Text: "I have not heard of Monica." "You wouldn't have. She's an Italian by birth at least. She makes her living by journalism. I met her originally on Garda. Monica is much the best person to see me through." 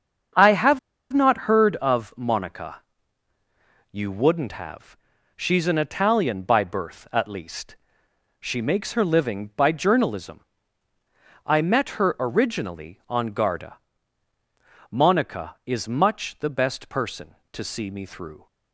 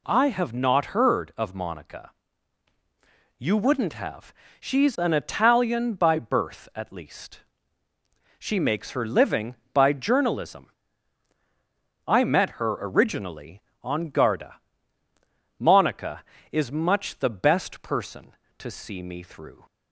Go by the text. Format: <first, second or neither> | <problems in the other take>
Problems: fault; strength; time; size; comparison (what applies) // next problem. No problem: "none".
second | starts louder than the rest; until 1.6 s; 7 dB // pauses between "have" and "not"; slight; at 0.7 s; 0.32 s long